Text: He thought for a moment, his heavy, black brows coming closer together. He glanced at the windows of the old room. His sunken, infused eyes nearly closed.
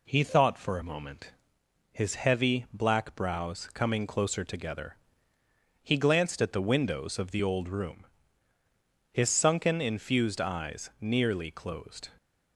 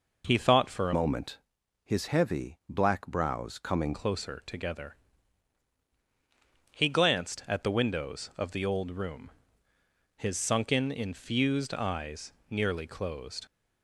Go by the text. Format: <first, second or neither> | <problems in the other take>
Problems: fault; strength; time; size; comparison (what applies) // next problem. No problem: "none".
first | changes voice from "moment" to "coming"; from 0.9 to 3.9 s; 3.0 s long // pauses between "eyes" and "nearly"; slight; at 12.3 s; 0.18 s long